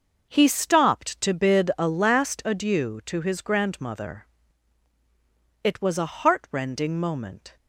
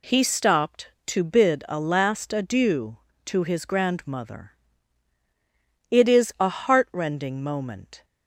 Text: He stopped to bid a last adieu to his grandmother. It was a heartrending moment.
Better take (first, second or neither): first